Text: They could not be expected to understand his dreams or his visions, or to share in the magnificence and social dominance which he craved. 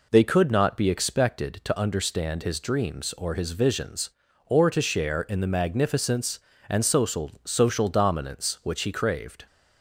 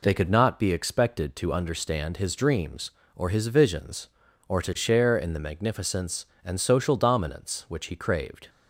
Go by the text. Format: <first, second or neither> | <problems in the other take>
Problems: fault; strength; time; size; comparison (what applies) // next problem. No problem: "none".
second | says "social" twice; at 7.4 s